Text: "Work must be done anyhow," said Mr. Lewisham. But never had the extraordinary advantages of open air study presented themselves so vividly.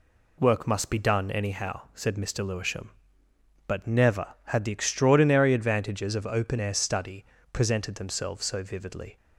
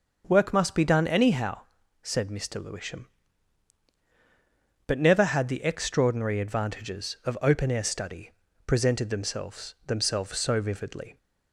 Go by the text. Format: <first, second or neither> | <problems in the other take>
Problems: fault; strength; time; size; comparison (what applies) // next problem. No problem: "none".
first | starts louder than the rest; until 1.2 s; 6.5 dB // pauses between "study" and "presented"; slight; at 8.3 s; 0.34 s long; slight in the first // says "themselves" twice; at 9.8 s